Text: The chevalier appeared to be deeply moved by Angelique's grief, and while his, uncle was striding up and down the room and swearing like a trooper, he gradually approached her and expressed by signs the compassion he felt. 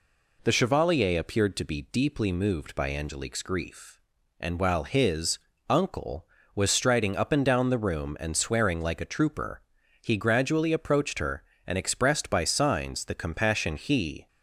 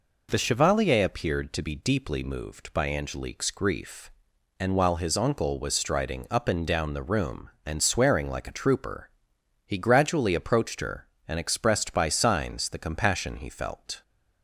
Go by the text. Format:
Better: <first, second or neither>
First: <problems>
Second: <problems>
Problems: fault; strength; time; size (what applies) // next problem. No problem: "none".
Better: second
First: stops before "felt"; at 14.2 s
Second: none